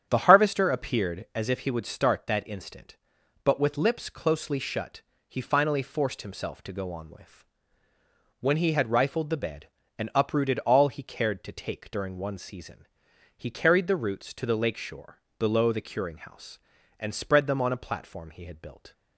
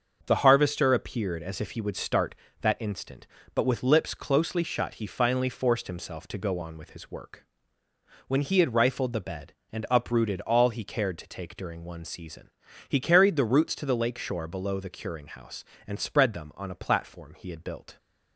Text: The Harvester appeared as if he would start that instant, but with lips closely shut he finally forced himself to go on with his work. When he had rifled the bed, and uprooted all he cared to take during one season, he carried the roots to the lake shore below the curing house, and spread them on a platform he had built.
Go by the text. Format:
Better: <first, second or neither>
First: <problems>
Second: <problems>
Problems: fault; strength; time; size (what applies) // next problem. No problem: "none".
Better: second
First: starts louder than the rest; strong; until 1.0 s; 8.5 dB // pauses between "shut" and "he"; slight; at 5.0 s; 0.30 s long // skips "his work"; at 7.9 s // pauses between "shore" and "below"; slight; at 15.1 s; 0.20 s long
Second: starts louder than the rest; until 1.2 s; 6.5 dB